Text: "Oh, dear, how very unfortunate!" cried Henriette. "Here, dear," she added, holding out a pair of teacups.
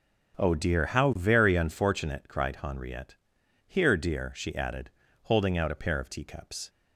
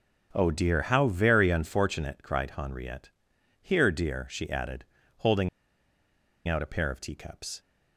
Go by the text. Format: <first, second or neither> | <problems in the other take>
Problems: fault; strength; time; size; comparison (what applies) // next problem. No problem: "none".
first | starts louder than the rest; until 1.3 s; 6.5 dB; also in the first // pauses between "holding" and "out"; at 5.4 s; 0.99 s long